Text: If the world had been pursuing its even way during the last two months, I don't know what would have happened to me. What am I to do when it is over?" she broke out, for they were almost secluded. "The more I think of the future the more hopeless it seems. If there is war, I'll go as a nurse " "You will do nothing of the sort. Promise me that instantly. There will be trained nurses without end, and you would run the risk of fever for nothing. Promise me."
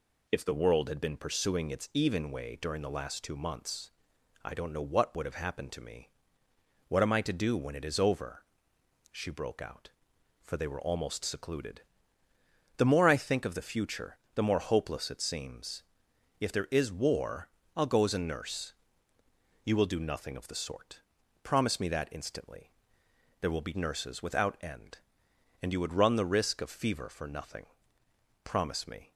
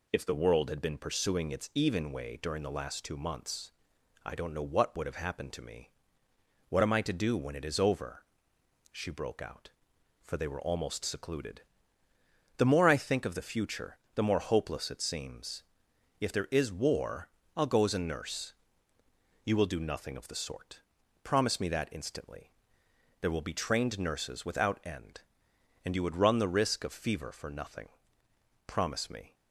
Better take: second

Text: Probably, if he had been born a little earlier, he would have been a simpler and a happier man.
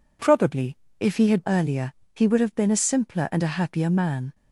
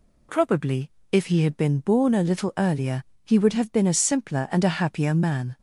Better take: second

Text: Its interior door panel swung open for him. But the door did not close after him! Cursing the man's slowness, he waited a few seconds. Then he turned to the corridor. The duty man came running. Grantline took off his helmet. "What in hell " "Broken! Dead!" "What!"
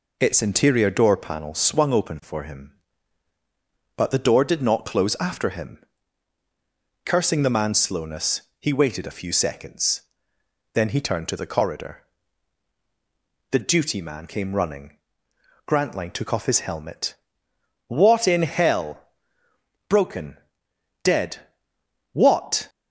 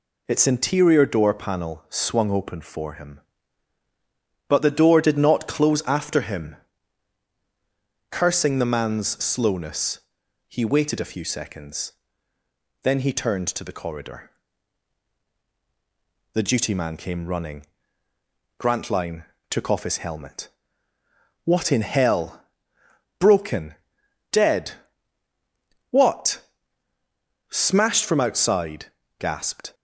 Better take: first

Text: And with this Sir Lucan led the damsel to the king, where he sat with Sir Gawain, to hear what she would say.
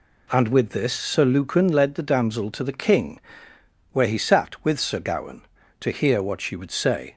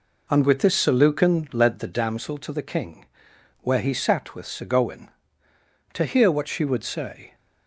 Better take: first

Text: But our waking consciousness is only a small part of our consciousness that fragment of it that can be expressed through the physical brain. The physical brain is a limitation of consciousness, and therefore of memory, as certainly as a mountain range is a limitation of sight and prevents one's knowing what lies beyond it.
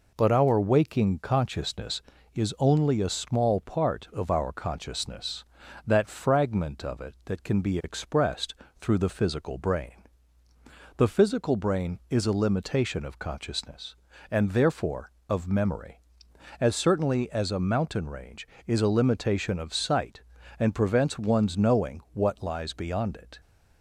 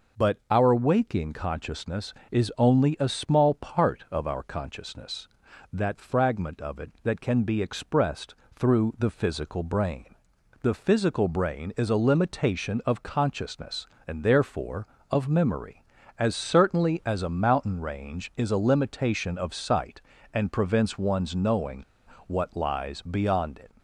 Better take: first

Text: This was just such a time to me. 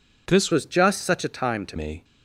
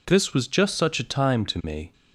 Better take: second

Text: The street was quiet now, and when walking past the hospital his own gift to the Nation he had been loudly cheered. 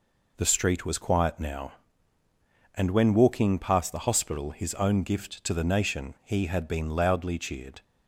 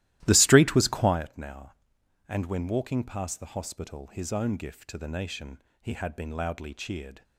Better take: first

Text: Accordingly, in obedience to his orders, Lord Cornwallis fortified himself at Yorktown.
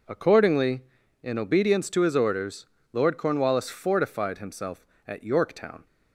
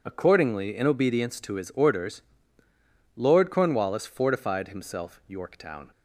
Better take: first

